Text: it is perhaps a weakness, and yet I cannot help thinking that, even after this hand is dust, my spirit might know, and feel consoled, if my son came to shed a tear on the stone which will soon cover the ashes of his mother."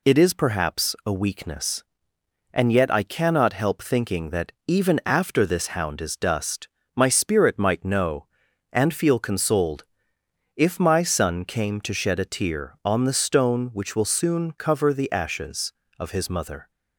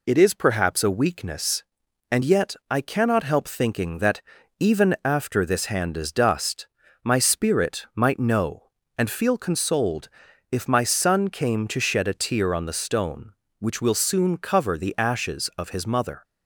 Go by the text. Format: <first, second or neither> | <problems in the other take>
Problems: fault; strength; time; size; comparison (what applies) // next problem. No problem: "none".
second | says "hound" for "hand"; at 5.6 s